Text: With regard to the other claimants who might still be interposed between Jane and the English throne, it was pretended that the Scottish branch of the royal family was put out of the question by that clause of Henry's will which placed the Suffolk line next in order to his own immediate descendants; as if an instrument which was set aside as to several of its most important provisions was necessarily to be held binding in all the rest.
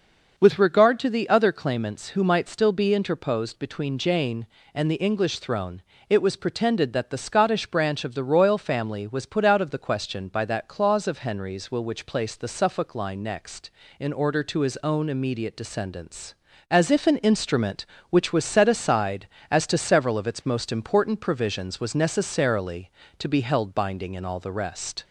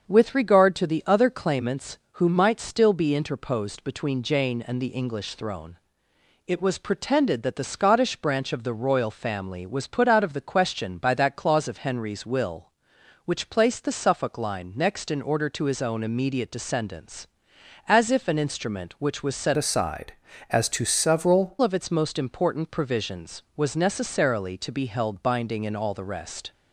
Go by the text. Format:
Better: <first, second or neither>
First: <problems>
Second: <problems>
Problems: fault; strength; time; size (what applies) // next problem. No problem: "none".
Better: first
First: starts louder than the rest; noticeable; until 1.4 s; 6 dB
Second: starts louder than the rest; until 1.1 s; 7 dB // changes voice from "aside" to "several"; from 19.5 to 21.5 s; 2.0 s long